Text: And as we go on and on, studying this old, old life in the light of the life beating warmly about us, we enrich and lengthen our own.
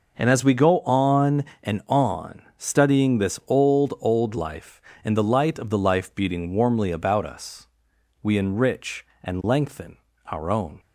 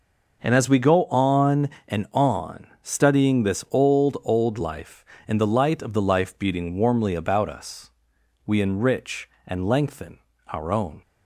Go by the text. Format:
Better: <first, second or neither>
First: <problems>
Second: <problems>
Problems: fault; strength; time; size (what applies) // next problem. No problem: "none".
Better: neither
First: pauses between "lengthen" and "our"; slight; at 9.9 s; 0.28 s long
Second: pauses between "lengthen" and "our"; slight; at 10.1 s; 0.28 s long